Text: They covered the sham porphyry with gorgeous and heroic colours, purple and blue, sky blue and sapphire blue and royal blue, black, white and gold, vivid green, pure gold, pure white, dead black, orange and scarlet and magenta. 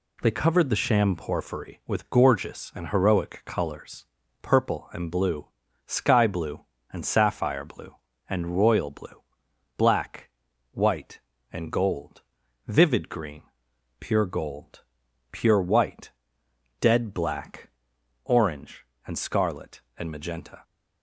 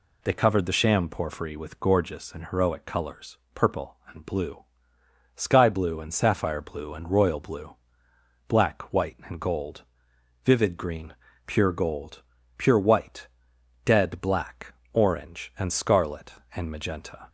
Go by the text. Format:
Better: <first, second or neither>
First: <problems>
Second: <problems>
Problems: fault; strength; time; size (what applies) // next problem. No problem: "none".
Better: neither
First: none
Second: none